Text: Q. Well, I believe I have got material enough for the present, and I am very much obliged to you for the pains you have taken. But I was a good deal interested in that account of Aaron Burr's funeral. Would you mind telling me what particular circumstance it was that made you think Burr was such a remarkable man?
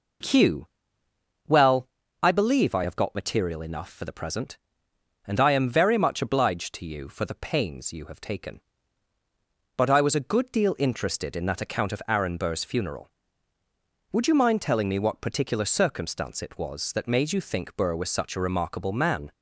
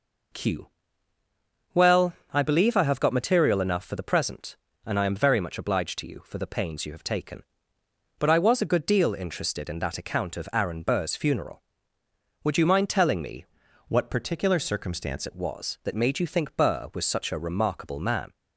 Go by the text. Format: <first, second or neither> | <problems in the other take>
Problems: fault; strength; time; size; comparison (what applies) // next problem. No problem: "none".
first | changes voice from "what" to "circumstance"; from 13.8 to 15.2 s; 1.4 s long